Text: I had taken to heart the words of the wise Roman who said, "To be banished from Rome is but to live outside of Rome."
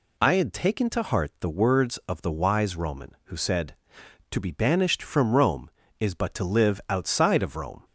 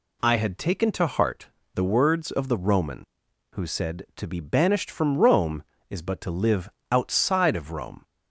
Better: first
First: none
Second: pauses between "heart" and "the"; slight; at 1.4 s; 0.28 s long // skips "wise"; at 2.5 s // pauses between "live" and "outside"; slight; at 6.6 s; 0.22 s long

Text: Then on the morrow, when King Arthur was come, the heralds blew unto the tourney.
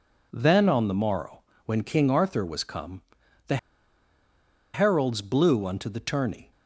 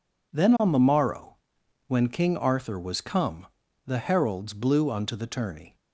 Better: second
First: pauses between "the" and "heralds"; at 3.5 s; 1.1 s long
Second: none

